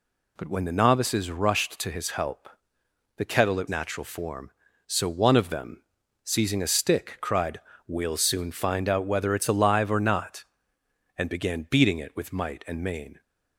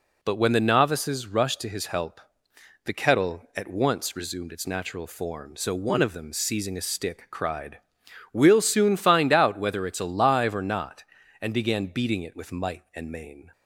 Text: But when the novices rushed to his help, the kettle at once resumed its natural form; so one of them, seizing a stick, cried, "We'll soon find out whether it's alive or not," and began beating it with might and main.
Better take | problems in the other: second | skips "once resumed its"; at 3.6 s

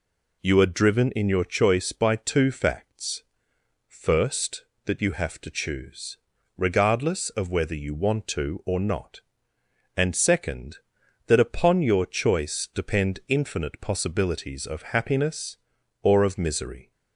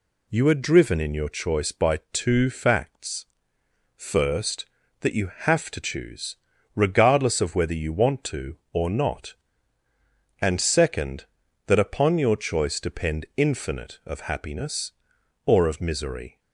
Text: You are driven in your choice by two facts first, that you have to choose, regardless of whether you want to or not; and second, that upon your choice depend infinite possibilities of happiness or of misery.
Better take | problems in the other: first | pauses between "facts" and "first"; noticeable; at 3.2 s; 0.70 s long; noticeable in the first // skips "possibilities"; at 14.0 s

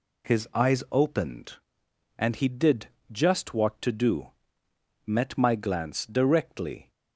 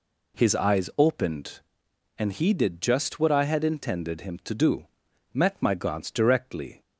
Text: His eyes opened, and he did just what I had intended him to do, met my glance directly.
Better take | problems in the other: second | pauses between "did" and "just"; slight; at 2.8 s; 0.24 s long // skips "I had intended him"; at 3.8 s

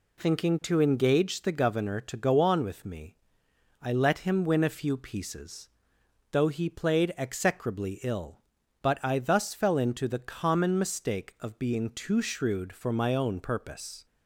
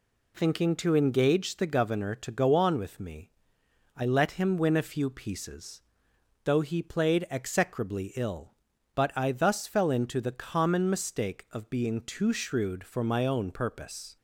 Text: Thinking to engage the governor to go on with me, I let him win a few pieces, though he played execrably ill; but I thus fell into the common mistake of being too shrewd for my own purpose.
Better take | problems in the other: neither | none

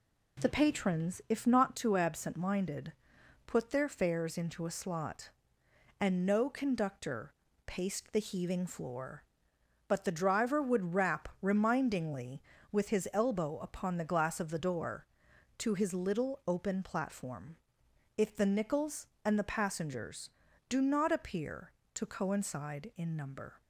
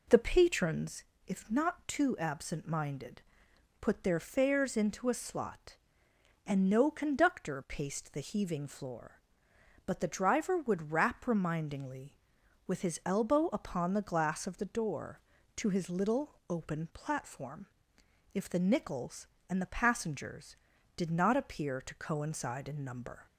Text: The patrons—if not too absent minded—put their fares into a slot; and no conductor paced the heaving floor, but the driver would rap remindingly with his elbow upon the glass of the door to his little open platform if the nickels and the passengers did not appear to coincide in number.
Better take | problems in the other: second | pauses between "conductor" and "paced"; slight; at 7.3 s; 0.32 s long // pauses between "platform" and "if"; noticeable; at 17.5 s; 0.62 s long; noticeable in the second // says "do" for "did"; at 20.6 s

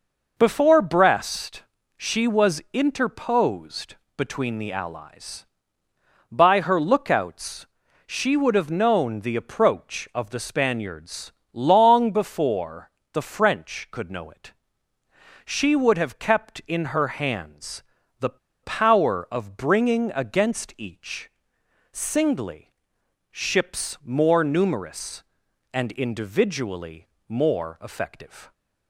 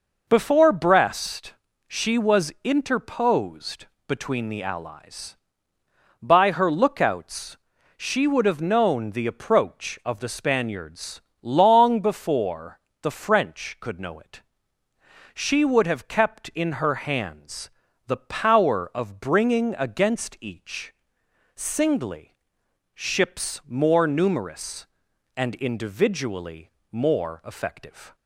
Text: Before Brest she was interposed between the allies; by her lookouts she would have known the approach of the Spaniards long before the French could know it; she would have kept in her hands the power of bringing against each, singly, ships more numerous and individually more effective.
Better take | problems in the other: second | pauses between "Brest" and "she"; slight; at 1.6 s; 0.32 s long; slight in the second // pauses between "interposed" and "between"; slight; at 3.9 s; 0.20 s long; slight in the second // pauses between "lookouts" and "she"; at 7.6 s; 0.40 s long; also in the second // pauses between "Spaniards" and "long"; slight; at 11.3 s; 0.20 s long; slight in the second // pauses between "before" and "the"; slight; at 12.9 s; 0.22 s long; slight in the second // pauses between "hands" and "the"; at 17.8 s; 0.38 s long; also in the second // pauses between "the" and "power"; slight; at 18.3 s; 0.25 s long // pauses between "individually" and "more"; slight; at 27.0 s; 0.20 s long; slight in the second

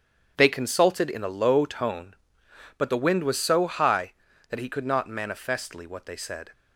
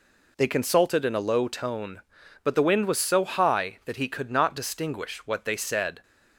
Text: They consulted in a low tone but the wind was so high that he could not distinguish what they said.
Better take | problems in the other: second | starts louder than the rest; strong; until 1.3 s; 8 dB // says "manifestly" for "distinguish"; at 5.0 s

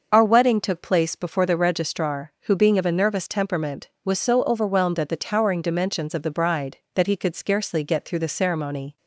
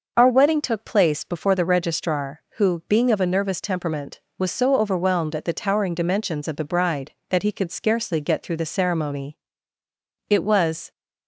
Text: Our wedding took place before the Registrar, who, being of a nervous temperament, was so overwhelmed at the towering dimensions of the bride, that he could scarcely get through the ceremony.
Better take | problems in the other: first | starts louder than the rest; until 1.1 s; 6 dB; noticeable in the first // goes on to say "It was"; noticeable; from 10.2 s on; 0.62 s long

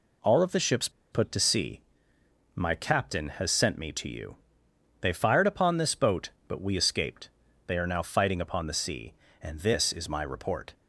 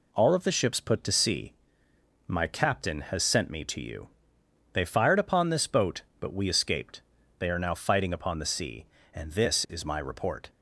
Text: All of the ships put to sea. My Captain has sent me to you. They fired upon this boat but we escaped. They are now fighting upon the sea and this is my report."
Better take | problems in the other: second | pauses between "ships" and "put"; slight; at 0.8 s; 0.22 s long

